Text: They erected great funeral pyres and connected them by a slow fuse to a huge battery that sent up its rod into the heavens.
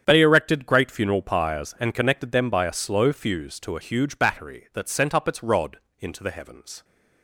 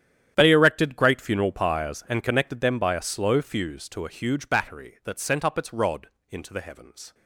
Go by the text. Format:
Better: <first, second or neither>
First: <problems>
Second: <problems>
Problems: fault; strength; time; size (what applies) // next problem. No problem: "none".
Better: first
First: starts louder than the rest; strong; until 1.0 s; 8.5 dB // pauses between "rod" and "into"; slight; at 5.7 s; 0.22 s long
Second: gets quieter; strong; throughout; 17 dB // starts louder than the rest; strong; until 1.3 s; 10 dB // pauses between "rod" and "into"; slight; at 6.0 s; 0.22 s long